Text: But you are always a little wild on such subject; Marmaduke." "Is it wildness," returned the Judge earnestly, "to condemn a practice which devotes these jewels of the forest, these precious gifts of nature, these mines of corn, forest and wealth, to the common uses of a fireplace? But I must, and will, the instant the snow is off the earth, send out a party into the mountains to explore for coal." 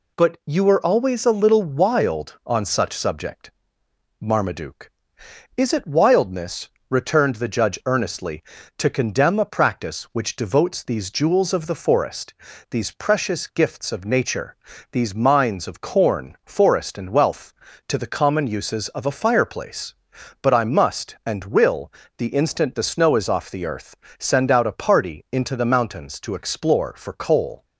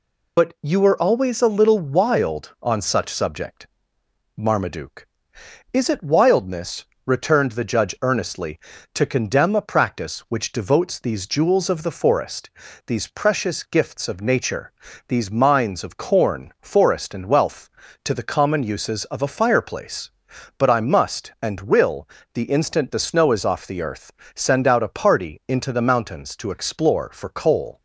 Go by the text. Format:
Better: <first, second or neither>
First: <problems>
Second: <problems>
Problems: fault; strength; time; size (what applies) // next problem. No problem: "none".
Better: first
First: none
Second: loses the start of "But"; at 0.3 s; 50 ms